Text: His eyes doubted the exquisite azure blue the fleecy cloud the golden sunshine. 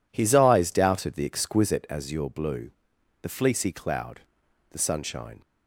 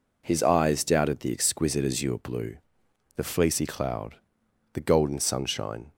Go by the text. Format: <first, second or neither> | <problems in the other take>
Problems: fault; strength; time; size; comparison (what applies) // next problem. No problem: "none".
second | pauses between "blue" and "the"; noticeable; at 2.7 s; 0.50 s long; noticeable in the second // pauses between "cloud" and "the"; noticeable; at 4.2 s; 0.50 s long; noticeable in the second // skips "golden"; at 4.7 s